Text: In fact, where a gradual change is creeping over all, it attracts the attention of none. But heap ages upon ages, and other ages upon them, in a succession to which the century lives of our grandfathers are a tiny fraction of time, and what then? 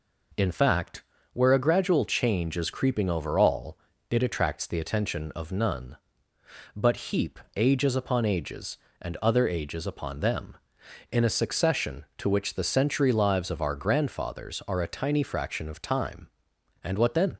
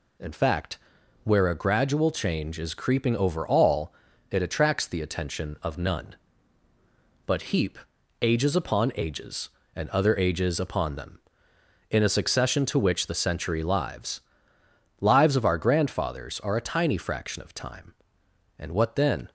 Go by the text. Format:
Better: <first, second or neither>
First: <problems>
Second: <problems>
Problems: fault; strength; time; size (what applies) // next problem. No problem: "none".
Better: first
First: pauses between "heap" and "ages"; slight; at 7.3 s; 0.18 s long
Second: pauses between "heap" and "ages"; at 7.7 s; 0.42 s long // says "lives" twice; at 15.0 s